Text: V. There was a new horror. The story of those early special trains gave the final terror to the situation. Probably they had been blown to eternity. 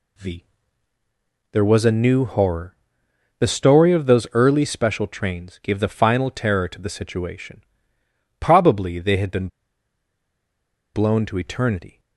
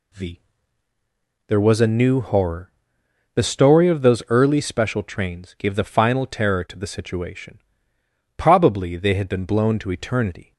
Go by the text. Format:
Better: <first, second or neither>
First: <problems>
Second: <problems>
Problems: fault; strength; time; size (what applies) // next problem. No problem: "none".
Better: second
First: pauses between "been" and "blown"; strong; at 9.4 s; 1.4 s long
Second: none